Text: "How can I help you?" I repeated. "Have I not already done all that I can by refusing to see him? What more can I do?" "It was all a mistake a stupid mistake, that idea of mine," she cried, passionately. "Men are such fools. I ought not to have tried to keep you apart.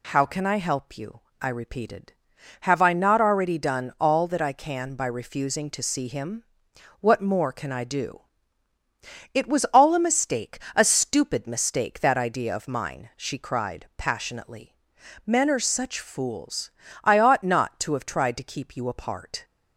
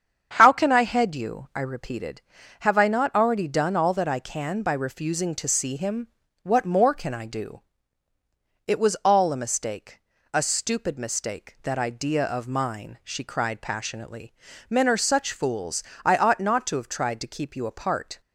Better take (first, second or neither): first